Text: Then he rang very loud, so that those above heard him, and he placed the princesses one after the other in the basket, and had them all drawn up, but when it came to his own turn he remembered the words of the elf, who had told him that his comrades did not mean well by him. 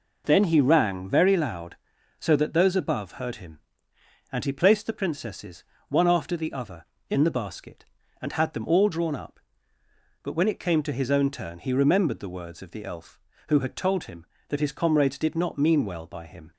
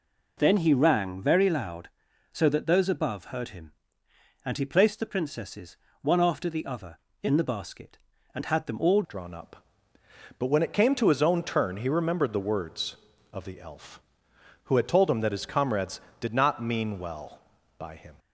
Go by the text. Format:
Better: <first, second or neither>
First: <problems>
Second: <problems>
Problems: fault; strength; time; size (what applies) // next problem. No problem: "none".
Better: first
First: pauses between "princesses" and "one"; slight; at 5.6 s; 0.24 s long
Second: pauses between "princesses" and "one"; slight; at 5.7 s; 0.24 s long // changes voice at "drawn"; from 9.0 s on; 9.1 s long